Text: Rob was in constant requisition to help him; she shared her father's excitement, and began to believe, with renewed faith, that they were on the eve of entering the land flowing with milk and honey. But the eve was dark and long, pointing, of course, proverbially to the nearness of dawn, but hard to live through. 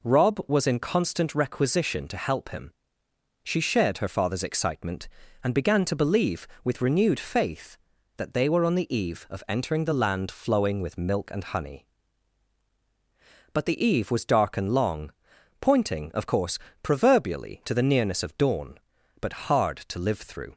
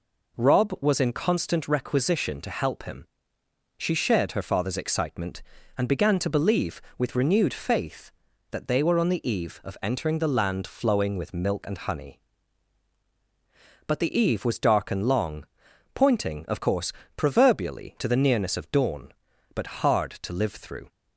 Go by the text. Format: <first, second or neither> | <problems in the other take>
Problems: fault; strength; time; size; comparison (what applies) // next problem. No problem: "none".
neither | none